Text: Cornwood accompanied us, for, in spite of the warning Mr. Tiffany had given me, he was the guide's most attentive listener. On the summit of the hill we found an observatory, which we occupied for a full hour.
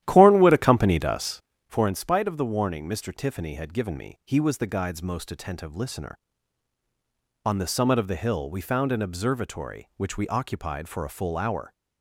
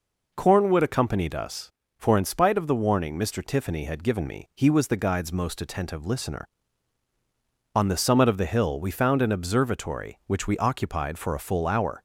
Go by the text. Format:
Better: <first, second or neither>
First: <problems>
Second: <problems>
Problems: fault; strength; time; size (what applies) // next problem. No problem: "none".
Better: second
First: starts louder than the rest; strong; until 1.8 s; 12.5 dB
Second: none